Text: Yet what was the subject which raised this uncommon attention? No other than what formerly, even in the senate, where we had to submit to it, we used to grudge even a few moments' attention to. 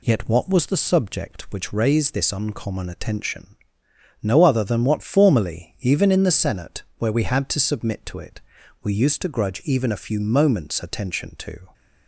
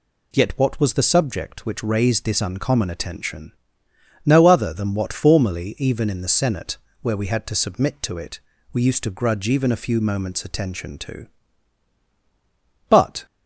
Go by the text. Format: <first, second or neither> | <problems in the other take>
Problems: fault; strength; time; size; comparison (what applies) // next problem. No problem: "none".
first | goes on to say "But"; slight; from 12.8 s on; 0.36 s long